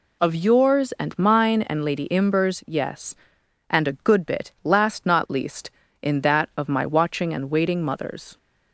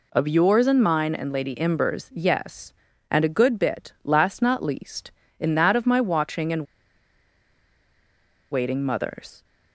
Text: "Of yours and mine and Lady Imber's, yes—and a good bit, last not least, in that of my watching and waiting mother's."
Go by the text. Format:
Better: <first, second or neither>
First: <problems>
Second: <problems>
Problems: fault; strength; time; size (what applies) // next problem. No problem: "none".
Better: first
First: none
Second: pauses between "and" and "waiting"; strong; at 6.6 s; 1.8 s long